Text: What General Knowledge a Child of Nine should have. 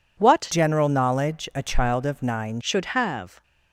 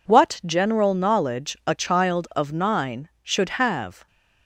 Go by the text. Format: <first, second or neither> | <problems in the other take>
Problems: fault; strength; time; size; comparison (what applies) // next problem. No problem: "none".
second | changes voice from "General" to "Nine"; from 0.5 to 2.6 s; 2.1 s long